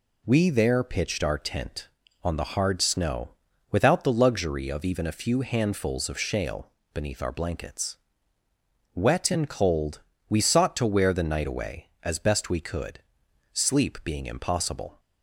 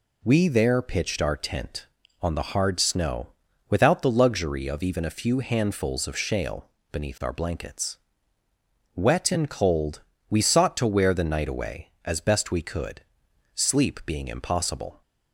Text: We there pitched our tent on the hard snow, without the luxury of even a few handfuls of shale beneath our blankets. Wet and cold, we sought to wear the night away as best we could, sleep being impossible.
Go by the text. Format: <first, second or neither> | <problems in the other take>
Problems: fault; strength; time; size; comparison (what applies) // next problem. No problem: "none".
neither | pauses between "shale" and "beneath"; slight; the same in both